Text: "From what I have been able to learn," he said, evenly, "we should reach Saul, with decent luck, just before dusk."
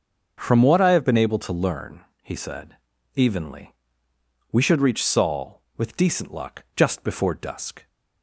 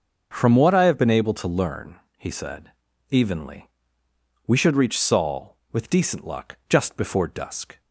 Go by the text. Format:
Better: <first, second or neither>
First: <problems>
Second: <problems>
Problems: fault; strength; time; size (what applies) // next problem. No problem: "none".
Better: neither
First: starts louder than the rest; until 1.3 s; 6.5 dB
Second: starts louder than the rest; until 1.3 s; 6.5 dB